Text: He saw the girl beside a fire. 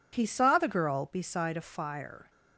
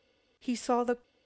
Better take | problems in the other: first | stops before "girl beside a fire"; at 1.0 s

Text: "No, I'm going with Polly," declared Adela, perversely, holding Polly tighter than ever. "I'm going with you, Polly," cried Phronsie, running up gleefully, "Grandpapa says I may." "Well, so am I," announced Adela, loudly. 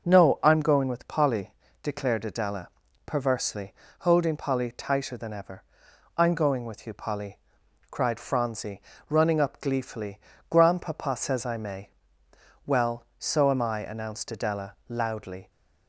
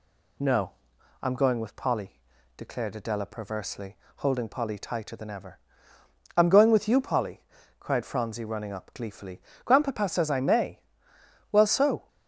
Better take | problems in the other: first | stops before "am I announced Adela loudly"; at 12.0 s

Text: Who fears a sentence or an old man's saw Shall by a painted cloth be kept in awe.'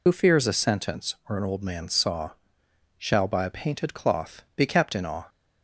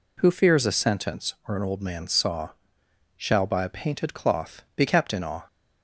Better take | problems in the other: second | loses the start of "Who"; at 0.0 s; 75 ms // pauses between "saw" and "Shall"; noticeable; at 2.2 s; 0.68 s long; noticeable in the second

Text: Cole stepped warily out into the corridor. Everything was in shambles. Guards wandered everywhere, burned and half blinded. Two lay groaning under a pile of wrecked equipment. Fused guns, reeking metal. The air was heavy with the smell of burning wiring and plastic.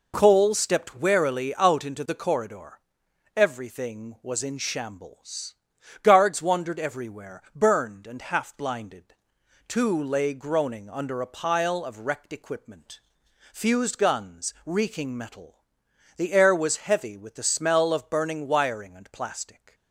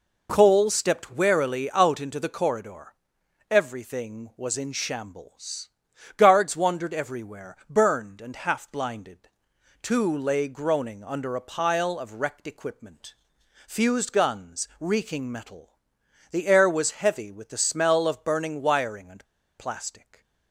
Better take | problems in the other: first | pauses between "and" and "plastic"; slight; at 19.2 s; 0.32 s long // stays silent after the last word; slight; from 19.9 s on; 0.6 s long

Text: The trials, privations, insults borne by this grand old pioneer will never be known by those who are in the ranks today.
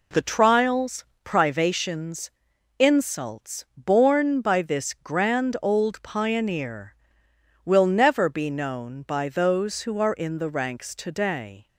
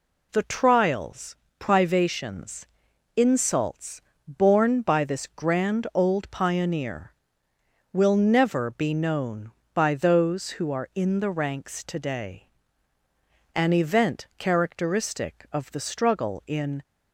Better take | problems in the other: first | pauses between "insults" and "borne"; slight; at 3.9 s; 0.28 s long // goes on to say "An event characteristic of the struggle in"; strong; from 13.5 s on; 3.2 s long

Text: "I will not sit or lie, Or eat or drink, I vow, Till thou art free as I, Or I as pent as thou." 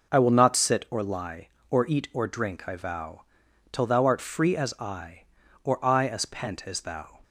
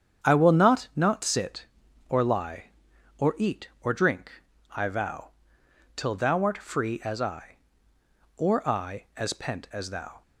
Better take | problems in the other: first | starts louder than the rest; strong; until 1.3 s; 8 dB // says "not" twice; at 0.9 s

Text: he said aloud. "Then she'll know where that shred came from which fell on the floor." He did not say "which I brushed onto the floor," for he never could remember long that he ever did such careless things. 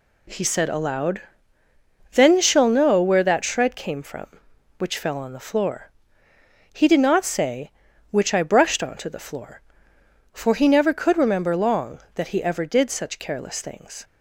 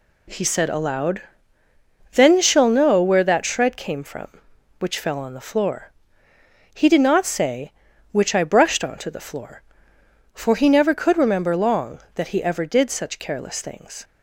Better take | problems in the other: neither | none

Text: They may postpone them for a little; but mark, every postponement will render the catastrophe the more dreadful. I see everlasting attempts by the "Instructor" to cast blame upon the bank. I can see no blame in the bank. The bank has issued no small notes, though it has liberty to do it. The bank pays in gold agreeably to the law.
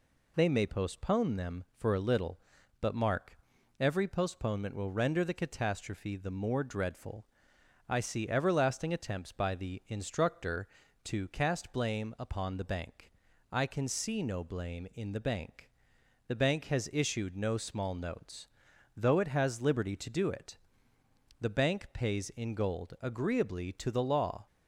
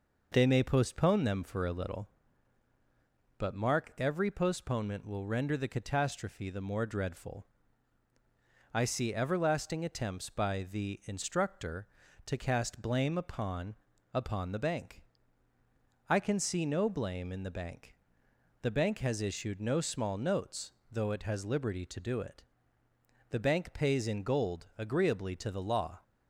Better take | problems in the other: first | says "upon" twice; at 14.1 s

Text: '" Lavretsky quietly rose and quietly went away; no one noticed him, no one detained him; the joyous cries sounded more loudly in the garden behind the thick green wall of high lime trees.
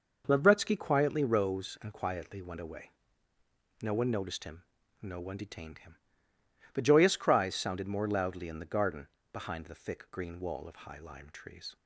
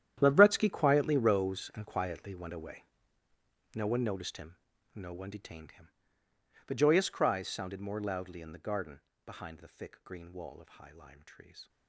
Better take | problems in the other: first | gets quieter; strong; throughout; 16.5 dB // pauses between "garden" and "behind"; slight; at 8.9 s; 0.26 s long; slight in the first

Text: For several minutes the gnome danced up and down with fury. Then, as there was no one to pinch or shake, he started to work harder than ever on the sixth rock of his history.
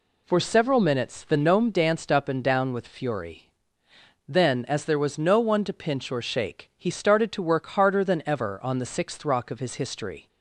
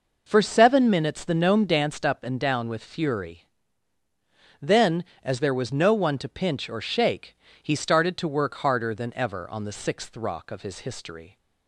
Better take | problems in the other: first | says "seven" for "several"; at 0.4 s

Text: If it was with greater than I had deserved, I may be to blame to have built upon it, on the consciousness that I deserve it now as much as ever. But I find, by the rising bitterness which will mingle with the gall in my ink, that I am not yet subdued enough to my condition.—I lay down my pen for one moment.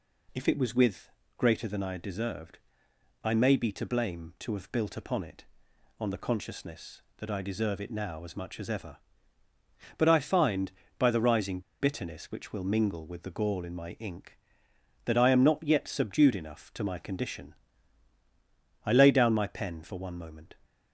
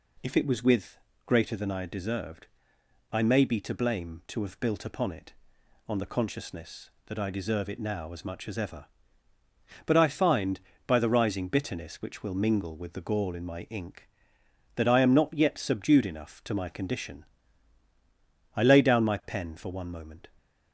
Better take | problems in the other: second | pauses between "with" and "greater"; slight; at 1.0 s; 0.28 s long; slight in the second // pauses between "rising" and "bitterness"; slight; at 11.5 s; 0.21 s long

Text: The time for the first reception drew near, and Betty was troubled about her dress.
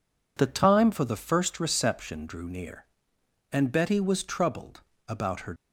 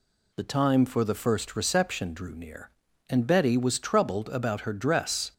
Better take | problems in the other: second | pauses between "troubled" and "about"; slight; at 4.8 s; 0.26 s long // stops before "dress"; at 5.5 s

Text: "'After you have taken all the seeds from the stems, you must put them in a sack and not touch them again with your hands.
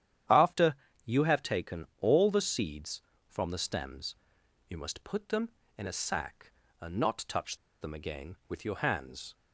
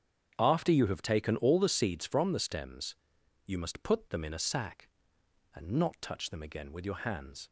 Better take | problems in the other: second | starts louder than the rest; strong; until 1.6 s; 10 dB; strong in the second // pauses between "After" and "you"; slight; at 0.7 s; 0.30 s long // pauses between "taken" and "all"; slight; at 1.8 s; 0.16 s long // pauses between "touch" and "them"; slight; at 7.5 s; 0.25 s long

